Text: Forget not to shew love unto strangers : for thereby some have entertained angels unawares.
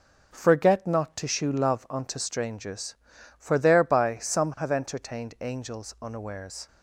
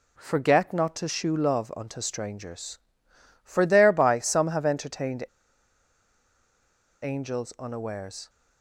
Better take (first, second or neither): first